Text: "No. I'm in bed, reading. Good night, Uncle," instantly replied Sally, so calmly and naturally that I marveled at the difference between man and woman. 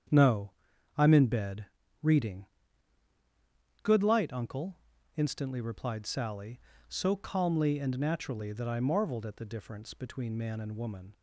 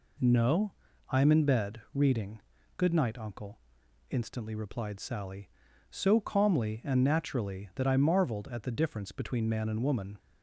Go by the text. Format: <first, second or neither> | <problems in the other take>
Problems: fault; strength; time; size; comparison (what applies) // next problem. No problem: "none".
second | starts louder than the rest; strong; until 1.5 s; 8 dB // says "light" for "night"; at 4.0 s